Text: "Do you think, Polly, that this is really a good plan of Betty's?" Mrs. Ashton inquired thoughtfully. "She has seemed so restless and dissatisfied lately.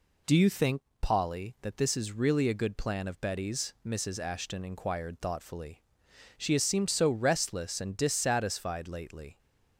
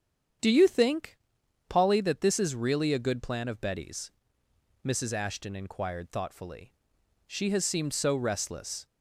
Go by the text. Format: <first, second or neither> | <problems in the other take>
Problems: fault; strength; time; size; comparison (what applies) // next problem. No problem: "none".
first | starts louder than the rest; strong; until 1.9 s; 8 dB // stops before "and dissatisfied lately"; at 8.8 s